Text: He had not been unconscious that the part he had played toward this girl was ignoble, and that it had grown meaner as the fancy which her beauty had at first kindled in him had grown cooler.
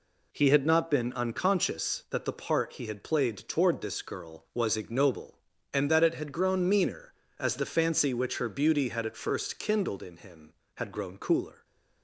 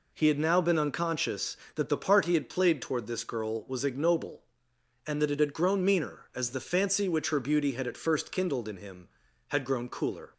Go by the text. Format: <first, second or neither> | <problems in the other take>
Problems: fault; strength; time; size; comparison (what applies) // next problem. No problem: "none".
first | says "now" for "not"; at 0.3 s